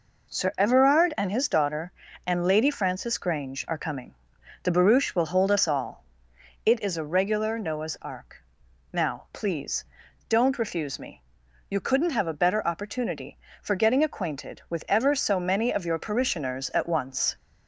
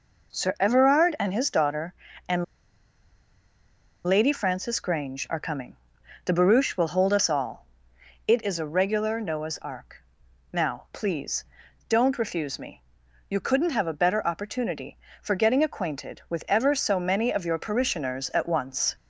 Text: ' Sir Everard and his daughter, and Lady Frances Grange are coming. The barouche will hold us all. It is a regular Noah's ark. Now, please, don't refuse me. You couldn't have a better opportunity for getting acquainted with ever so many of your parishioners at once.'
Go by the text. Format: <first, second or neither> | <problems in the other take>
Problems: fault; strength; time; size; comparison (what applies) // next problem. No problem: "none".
first | pauses between "and" and "Lady"; strong; at 2.4 s; 1.6 s long